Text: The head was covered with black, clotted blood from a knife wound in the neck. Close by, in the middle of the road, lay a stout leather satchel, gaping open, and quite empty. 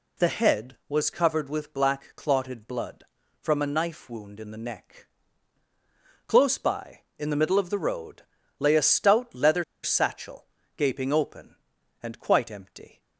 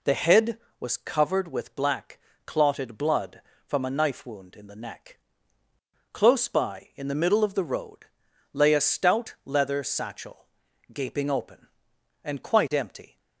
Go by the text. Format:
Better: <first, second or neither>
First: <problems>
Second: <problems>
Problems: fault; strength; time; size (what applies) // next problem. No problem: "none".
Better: second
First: pauses between "leather" and "satchel"; slight; at 9.6 s; 0.20 s long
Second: none